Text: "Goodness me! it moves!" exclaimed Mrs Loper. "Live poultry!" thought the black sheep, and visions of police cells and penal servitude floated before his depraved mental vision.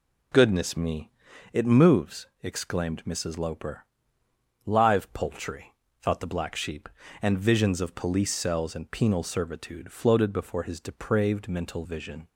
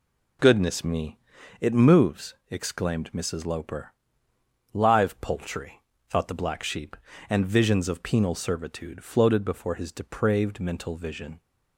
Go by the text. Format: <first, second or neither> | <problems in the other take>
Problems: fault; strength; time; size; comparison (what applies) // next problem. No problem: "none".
first | skips "police cells and"; at 8.0 s